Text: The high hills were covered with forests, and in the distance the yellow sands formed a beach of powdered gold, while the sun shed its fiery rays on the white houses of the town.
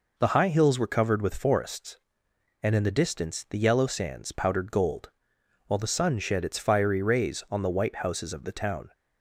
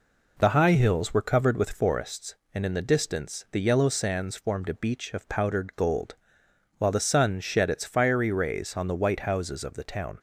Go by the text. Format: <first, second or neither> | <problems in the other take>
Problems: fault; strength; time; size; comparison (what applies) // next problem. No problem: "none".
second | skips "formed a beach of"; at 4.3 s